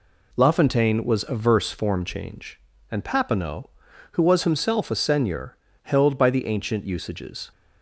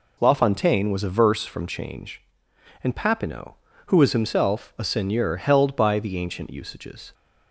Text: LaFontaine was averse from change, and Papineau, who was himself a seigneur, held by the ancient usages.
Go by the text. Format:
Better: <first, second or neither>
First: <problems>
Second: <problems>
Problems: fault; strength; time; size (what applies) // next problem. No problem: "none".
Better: second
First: says "form" for "from"; at 1.7 s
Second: none